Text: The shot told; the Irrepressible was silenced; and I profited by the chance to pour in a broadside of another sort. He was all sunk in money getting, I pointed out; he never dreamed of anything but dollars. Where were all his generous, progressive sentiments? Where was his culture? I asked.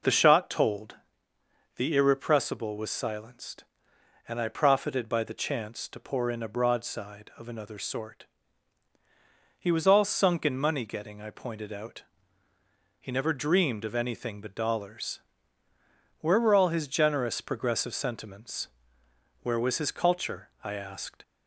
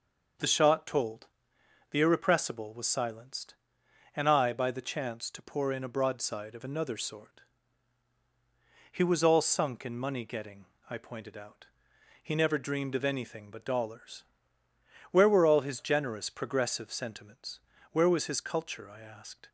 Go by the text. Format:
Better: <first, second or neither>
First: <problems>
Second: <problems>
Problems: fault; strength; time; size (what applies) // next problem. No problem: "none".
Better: first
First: none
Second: skips "profited"; at 4.5 s